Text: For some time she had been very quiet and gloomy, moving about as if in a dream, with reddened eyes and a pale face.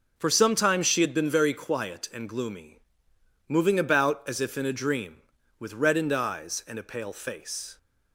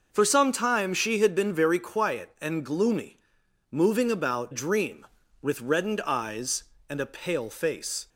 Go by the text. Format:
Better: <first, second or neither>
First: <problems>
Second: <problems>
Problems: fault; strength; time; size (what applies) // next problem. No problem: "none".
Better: first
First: none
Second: skips "as if in a"; at 4.5 s